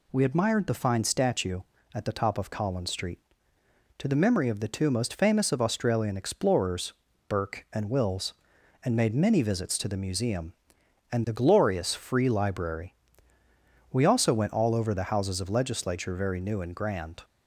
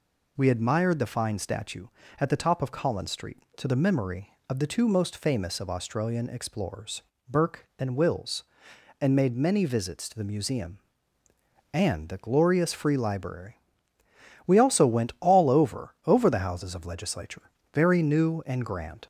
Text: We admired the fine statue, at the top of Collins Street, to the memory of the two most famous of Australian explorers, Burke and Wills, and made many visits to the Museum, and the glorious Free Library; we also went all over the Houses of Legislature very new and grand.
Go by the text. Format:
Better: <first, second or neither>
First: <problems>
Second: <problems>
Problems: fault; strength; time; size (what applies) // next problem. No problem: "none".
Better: first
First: none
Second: says "over" twice; at 16.0 s // pauses between "Legislature" and "very"; slight; at 17.4 s; 0.30 s long